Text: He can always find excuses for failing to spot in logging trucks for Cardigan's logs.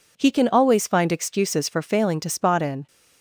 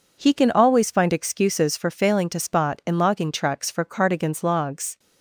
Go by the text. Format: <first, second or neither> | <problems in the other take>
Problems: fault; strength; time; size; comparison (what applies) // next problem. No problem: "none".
second | stops before "logging trucks for Cardigan's logs"; at 2.8 s